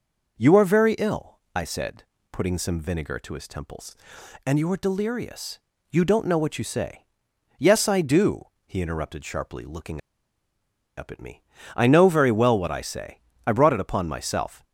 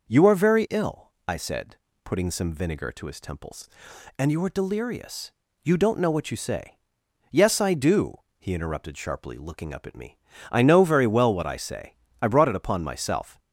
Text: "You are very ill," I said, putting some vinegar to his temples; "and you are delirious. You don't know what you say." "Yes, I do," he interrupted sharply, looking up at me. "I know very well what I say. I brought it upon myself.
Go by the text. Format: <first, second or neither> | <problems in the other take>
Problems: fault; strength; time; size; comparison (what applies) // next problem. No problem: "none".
second | pauses between "looking" and "up"; noticeable; at 9.9 s; 0.97 s long